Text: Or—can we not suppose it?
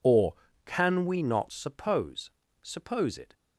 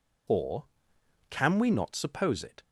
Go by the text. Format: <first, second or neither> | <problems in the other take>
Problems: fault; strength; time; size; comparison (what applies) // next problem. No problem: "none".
second | says "suppose" twice; at 2.6 s